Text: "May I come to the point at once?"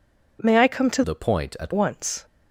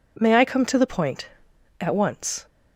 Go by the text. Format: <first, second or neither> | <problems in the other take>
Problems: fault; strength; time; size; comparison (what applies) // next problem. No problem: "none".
second | changes voice from "the" to "at"; from 1.0 to 1.7 s; 0.7 s long